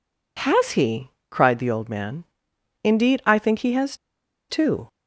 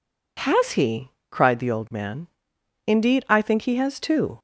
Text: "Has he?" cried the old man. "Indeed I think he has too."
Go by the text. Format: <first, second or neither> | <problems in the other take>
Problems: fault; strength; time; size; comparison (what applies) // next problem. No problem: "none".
second | pauses between "has" and "too"; noticeable; at 3.9 s; 0.54 s long